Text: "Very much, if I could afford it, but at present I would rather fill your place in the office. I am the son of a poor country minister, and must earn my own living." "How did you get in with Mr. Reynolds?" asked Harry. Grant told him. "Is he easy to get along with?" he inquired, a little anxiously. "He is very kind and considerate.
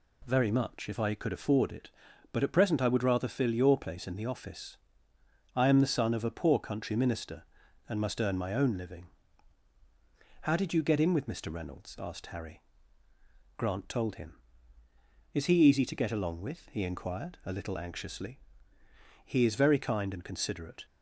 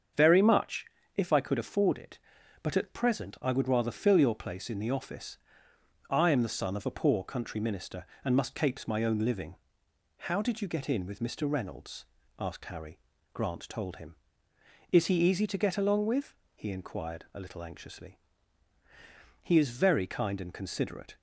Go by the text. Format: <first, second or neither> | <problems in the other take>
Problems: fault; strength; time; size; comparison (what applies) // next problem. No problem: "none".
first | starts louder than the rest; until 1.4 s; 7 dB // says "capes" for "earn"; at 8.5 s